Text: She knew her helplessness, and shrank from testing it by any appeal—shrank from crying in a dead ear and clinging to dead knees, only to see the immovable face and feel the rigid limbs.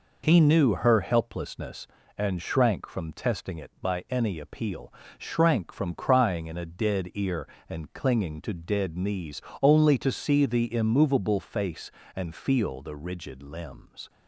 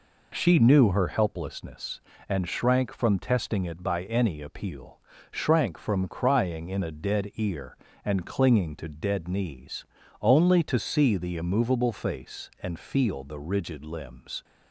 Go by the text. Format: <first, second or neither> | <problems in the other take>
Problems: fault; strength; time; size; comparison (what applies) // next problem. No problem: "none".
second | says "He" for "She"; at 0.2 s